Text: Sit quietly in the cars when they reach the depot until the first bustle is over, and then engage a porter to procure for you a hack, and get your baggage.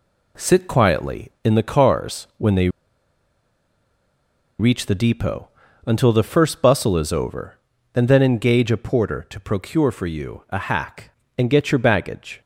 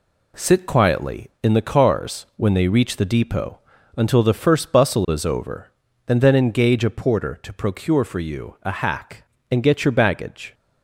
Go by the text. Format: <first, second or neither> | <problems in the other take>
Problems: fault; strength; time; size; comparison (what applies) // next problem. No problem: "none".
second | pauses between "they" and "reach"; strong; at 2.6 s; 1.9 s long // pauses between "depot" and "until"; slight; at 5.4 s; 0.36 s long; slight in the second